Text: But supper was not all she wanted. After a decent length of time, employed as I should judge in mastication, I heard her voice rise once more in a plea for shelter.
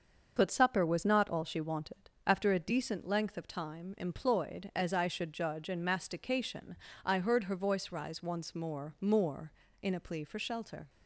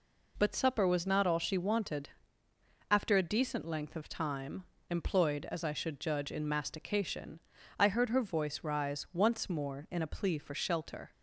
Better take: second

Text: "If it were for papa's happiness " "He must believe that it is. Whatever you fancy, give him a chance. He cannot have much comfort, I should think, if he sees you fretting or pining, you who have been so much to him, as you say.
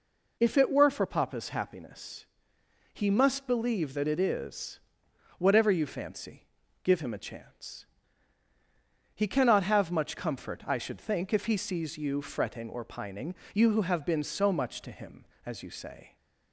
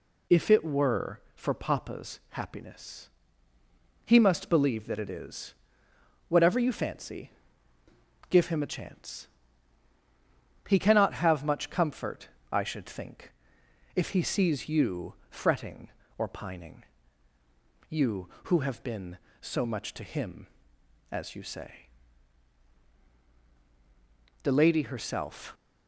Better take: first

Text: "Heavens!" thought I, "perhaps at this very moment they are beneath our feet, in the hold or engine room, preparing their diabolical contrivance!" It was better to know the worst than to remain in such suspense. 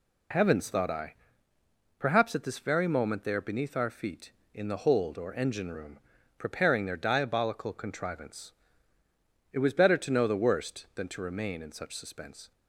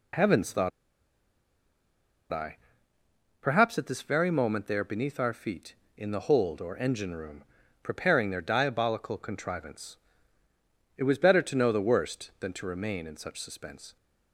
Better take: first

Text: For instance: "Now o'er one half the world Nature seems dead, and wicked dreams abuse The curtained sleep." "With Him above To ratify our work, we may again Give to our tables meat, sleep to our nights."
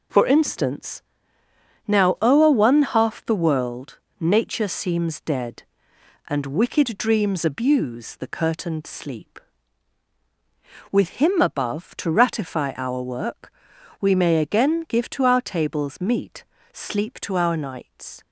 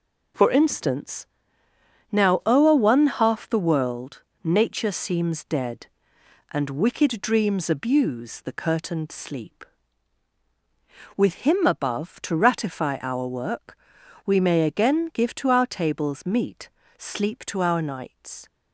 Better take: neither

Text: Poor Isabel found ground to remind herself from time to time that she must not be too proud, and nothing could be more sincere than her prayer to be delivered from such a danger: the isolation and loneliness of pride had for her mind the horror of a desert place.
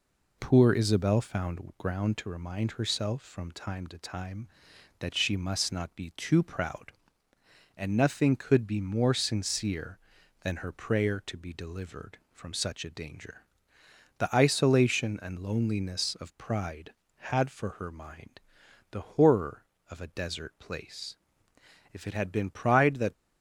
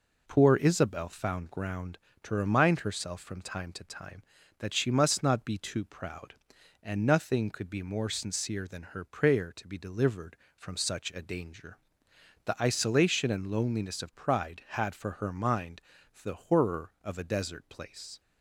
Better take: second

